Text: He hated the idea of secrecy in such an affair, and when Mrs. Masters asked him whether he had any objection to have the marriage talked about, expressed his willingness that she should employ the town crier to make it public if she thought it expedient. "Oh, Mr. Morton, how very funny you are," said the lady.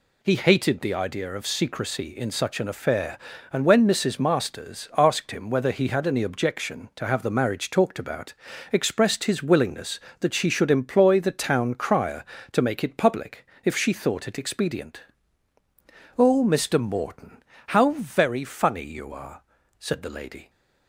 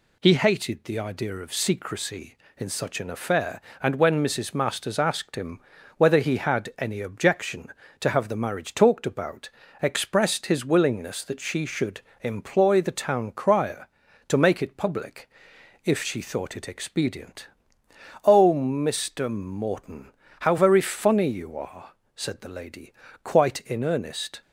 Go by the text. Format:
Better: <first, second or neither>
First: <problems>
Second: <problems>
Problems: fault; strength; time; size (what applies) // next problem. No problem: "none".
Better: first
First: pauses between "public" and "if"; slight; at 13.4 s; 0.18 s long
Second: pauses between "him" and "whether"; slight; at 5.6 s; 0.36 s long // pauses between "should" and "employ"; slight; at 12.0 s; 0.22 s long // pauses between "public" and "if"; noticeable; at 15.3 s; 0.54 s long // goes on to say "Quite in earnest"; noticeable; from 23.2 s on; 1.1 s long